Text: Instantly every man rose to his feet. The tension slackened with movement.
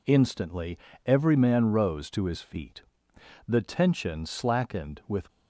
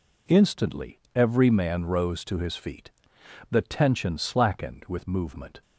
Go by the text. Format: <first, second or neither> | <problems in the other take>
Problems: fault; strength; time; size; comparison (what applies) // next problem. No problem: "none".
second | pauses between "Instantly" and "every"; slight; at 0.7 s; 0.28 s long; slight in the second // stops before "movement"; at 5.2 s